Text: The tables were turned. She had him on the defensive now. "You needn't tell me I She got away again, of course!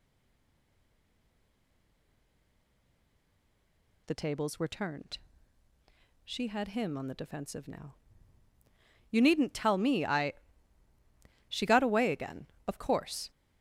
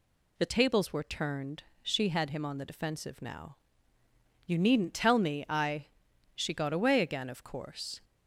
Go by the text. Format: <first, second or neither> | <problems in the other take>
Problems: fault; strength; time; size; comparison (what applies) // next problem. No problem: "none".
second | stays silent before the first word; strong; until 4.0 s; 4.0 s long // pauses between "I" and "She"; at 10.3 s; 1.1 s long; noticeable in the second